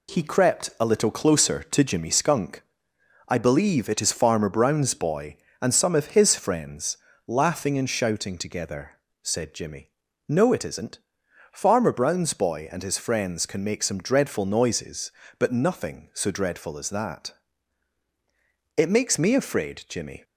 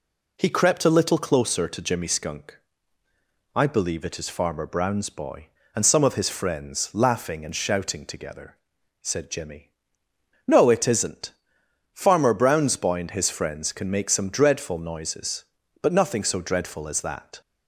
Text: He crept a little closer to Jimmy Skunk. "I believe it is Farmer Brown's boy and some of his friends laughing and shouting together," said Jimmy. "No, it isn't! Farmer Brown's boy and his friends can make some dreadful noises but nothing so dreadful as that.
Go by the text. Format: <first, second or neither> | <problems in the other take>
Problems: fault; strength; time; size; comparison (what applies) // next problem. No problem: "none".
second | pauses between "friends" and "laughing"; slight; at 6.9 s; 0.30 s long // goes on to say "It makes me afraid Jimmy"; from 18.7 s on; 1.4 s long